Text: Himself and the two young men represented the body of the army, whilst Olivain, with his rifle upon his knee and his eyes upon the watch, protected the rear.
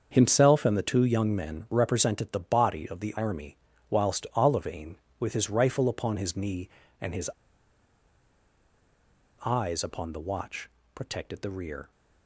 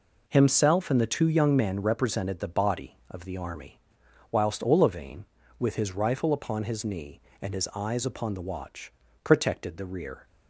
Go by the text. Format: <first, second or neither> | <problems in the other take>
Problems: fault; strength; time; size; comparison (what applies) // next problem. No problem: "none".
second | starts louder than the rest; until 1.1 s; 6.5 dB // pauses between "his" and "eyes"; strong; at 7.3 s; 2.1 s long